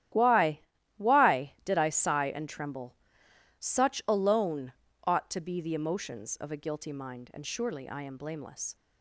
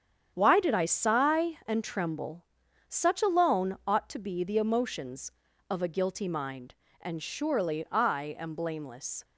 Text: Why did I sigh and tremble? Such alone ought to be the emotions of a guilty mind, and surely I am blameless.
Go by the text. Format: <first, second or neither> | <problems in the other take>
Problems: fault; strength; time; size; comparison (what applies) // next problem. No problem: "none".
second | starts louder than the rest; strong; until 1.5 s; 13 dB; strong in the second // says "Why" twice; at 0.9 s // pauses between "alone" and "ought"; slight; at 4.7 s; 0.34 s long